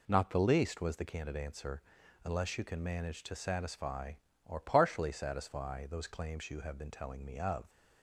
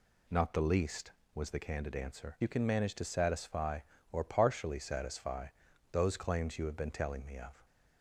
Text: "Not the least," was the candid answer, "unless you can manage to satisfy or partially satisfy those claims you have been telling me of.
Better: first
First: none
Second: skips "unless"; at 2.3 s // pauses between "satisfy" and "those"; at 5.4 s; 0.42 s long

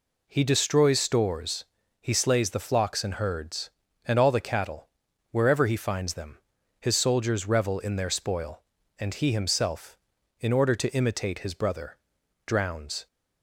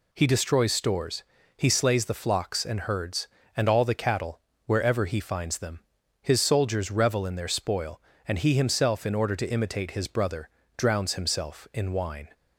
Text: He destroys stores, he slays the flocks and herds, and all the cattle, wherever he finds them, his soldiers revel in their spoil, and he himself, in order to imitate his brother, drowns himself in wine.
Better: second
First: stops before "himself in wine"; at 13.0 s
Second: none

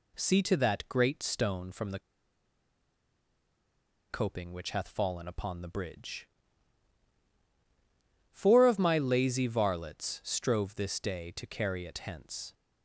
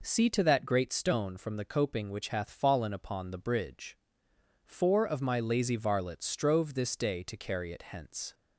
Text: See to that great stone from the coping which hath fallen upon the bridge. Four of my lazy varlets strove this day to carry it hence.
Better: second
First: pauses between "the" and "coping"; strong; at 1.9 s; 2.1 s long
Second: none

